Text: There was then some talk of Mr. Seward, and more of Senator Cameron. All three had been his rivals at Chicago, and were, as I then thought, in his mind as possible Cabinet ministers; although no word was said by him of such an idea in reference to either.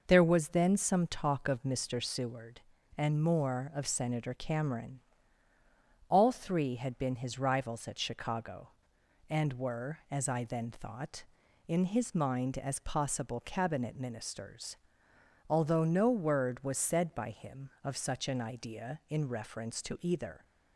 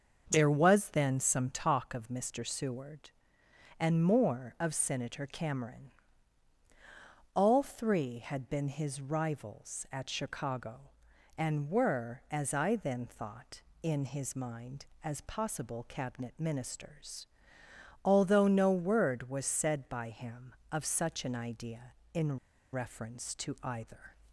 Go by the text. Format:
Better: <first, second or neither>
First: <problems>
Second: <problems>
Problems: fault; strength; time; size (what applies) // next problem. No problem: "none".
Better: first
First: none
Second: starts louder than the rest; until 1.3 s; 6.5 dB // pauses between "in" and "reference"; slight; at 22.3 s; 0.35 s long